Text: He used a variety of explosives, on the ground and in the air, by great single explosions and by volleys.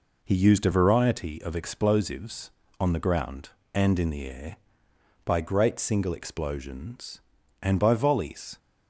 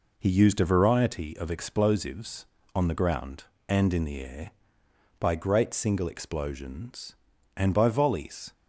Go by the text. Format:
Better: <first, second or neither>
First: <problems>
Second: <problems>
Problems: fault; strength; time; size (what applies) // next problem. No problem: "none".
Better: neither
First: none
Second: none